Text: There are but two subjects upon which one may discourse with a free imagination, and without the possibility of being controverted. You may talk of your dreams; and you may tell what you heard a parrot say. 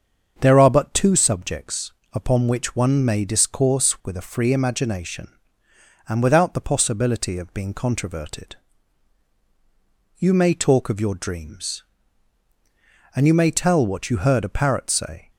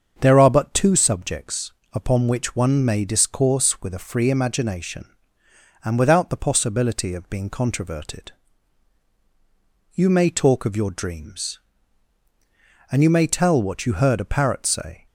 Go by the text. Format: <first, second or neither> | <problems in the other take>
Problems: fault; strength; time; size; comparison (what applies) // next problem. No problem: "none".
neither | starts louder than the rest; the same in both // pauses between "subjects" and "upon"; slight; the same in both